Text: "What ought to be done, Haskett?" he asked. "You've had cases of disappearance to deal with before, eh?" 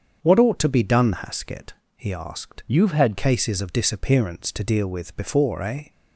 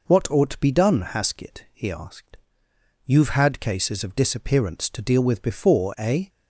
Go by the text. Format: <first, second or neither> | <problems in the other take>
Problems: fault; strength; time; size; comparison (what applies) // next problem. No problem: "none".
second | starts louder than the rest; strong; until 1.2 s; 7 dB // changes voice from "You've" to "had"; from 2.6 to 3.1 s; 0.5 s long